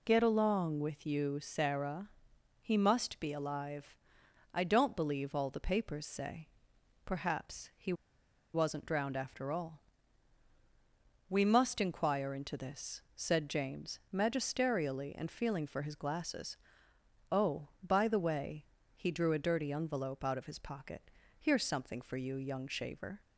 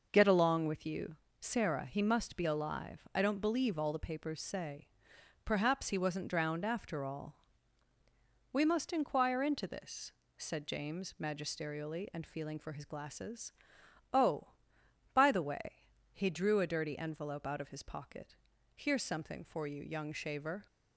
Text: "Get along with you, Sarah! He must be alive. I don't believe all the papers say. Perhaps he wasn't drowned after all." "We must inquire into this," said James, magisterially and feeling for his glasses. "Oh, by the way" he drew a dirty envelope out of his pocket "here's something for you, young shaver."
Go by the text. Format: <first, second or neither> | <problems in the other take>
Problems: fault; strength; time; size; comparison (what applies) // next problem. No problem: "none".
second | pauses between "he" and "wasn't"; noticeable; at 7.9 s; 0.61 s long // pauses between "way" and "he"; slight; at 18.6 s; 0.28 s long; slight in the second // pauses between "pocket" and "here's"; slight; at 21.0 s; 0.32 s long; also in the second